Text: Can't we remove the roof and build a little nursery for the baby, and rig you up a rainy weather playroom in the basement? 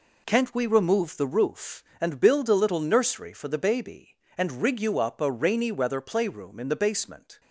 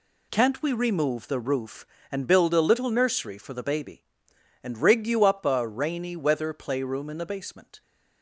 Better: neither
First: none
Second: none

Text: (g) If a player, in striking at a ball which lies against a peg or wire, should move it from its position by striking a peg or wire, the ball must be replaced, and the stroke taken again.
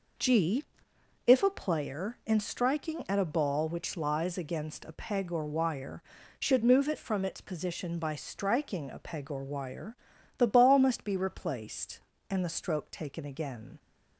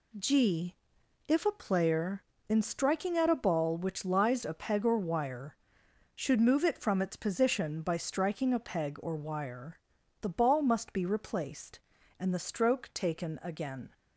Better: first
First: none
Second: skips "against"; at 4.4 s

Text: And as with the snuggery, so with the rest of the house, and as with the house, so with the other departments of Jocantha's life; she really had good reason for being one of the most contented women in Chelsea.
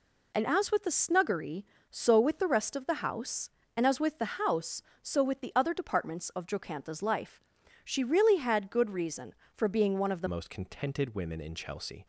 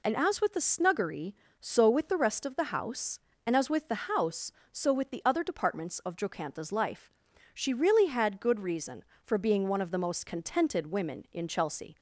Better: second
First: changes voice at "most"; from 10.2 s on; 1.8 s long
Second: none

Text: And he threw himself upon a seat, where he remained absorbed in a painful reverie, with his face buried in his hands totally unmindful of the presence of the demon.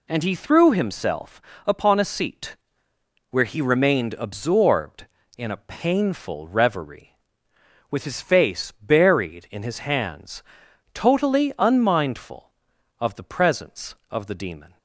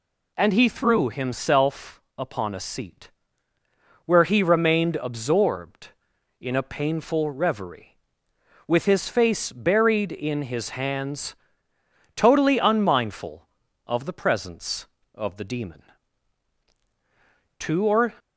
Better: first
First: pauses between "himself" and "upon"; slight; at 1.4 s; 0.24 s long // pauses between "hands" and "totally"; noticeable; at 10.4 s; 0.50 s long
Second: pauses between "himself" and "upon"; slight; at 2.0 s; 0.16 s long // pauses between "hands" and "totally"; noticeable; at 11.3 s; 0.80 s long // goes on to say "Two or"; from 17.5 s on; 0.54 s long

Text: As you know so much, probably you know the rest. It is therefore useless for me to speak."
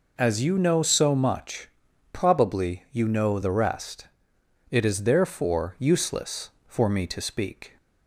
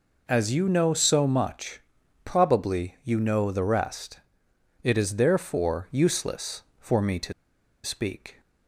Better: first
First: none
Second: pauses between "to" and "speak"; noticeable; at 7.3 s; 0.51 s long

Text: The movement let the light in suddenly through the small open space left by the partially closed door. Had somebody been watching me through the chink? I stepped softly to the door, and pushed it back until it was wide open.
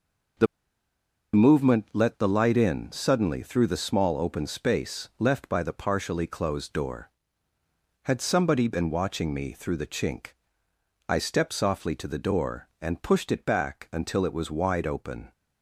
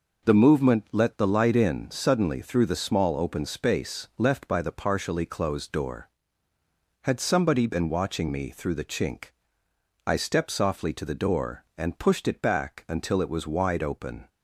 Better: second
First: pauses between "The" and "movement"; noticeable; at 0.4 s; 0.89 s long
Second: none

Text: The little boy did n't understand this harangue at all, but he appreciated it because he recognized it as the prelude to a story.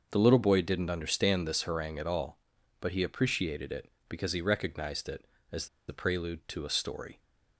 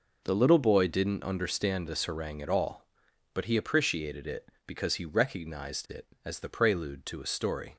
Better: second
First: starts louder than the rest; noticeable; until 1.1 s; 6 dB // pauses between "as" and "the"; slight; at 5.6 s; 0.21 s long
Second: none

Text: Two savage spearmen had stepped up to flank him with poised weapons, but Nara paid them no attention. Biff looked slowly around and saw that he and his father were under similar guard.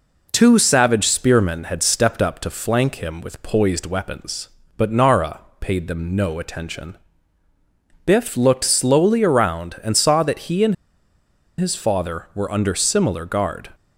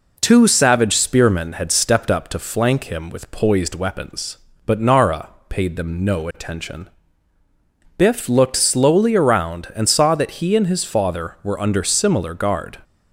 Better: second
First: pauses between "Nara" and "paid"; slight; at 5.4 s; 0.18 s long // pauses between "and" and "his"; noticeable; at 10.7 s; 0.83 s long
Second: pauses between "Nara" and "paid"; slight; at 5.3 s; 0.18 s long

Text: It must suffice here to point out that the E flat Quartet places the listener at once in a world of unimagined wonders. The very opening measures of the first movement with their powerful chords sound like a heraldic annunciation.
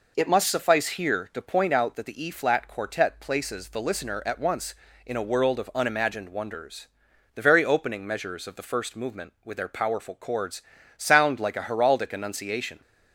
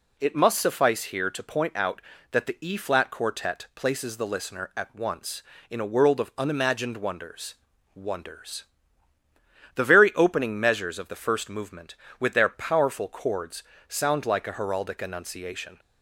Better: first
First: pauses between "chords" and "sound"; slight; at 10.6 s; 0.34 s long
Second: says "wonders" twice; at 7.9 s // pauses between "chords" and "sound"; slight; at 13.6 s; 0.28 s long

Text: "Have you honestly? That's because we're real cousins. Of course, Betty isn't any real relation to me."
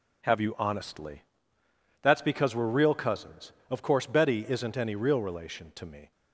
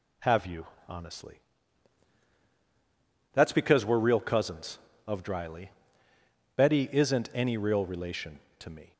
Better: first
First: none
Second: pauses between "you" and "honestly"; slight; at 0.6 s; 0.22 s long // says "dryly" for "course"; at 5.2 s

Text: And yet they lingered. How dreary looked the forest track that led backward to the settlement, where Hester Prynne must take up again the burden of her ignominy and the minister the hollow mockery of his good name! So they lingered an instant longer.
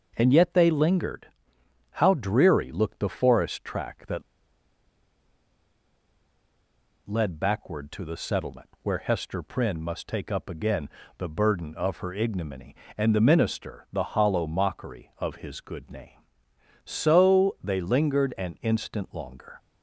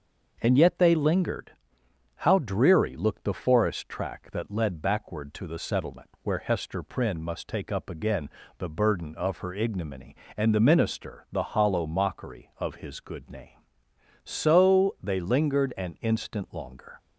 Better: second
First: starts louder than the rest; until 1.1 s; 6 dB // pauses between "that" and "led"; strong; at 4.2 s; 2.8 s long // pauses between "again" and "the"; slight; at 10.8 s; 0.30 s long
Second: starts louder than the rest; until 1.4 s; 6 dB // pauses between "again" and "the"; slight; at 8.2 s; 0.30 s long

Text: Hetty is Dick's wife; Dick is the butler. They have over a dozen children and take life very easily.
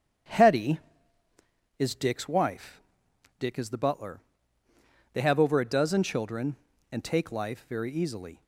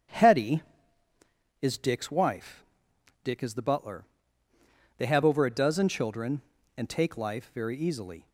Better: neither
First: starts louder than the rest; strong; until 2.2 s; 9 dB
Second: starts louder than the rest; strong; until 2.1 s; 9 dB

